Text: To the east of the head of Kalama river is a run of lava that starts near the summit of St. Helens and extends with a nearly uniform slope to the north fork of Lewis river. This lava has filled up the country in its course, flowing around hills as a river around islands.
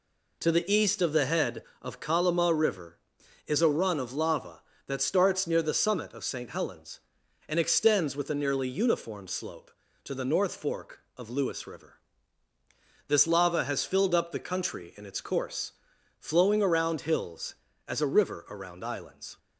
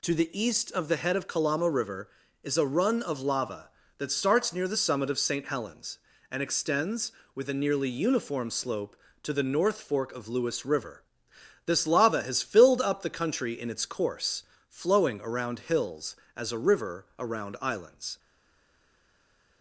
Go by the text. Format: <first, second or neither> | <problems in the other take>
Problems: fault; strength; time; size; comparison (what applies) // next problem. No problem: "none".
first | stays silent after the last word; noticeable; from 18.1 s on; 1.5 s long